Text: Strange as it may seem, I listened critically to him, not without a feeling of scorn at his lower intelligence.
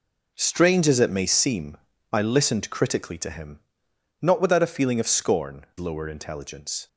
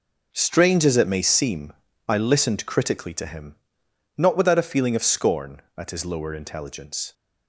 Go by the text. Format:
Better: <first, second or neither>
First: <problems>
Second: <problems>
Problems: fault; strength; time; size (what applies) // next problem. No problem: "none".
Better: second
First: skips "at his"; at 5.7 s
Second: none